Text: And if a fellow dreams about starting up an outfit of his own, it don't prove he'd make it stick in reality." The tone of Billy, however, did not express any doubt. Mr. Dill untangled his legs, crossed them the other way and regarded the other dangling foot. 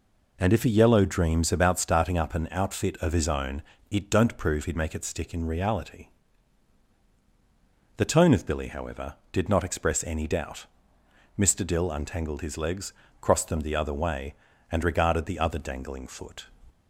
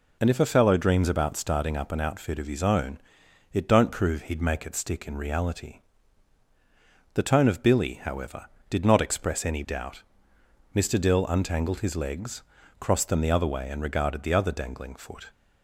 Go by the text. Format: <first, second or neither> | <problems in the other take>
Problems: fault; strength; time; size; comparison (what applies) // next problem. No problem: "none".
second | says "yellow" for "fellow"; at 0.6 s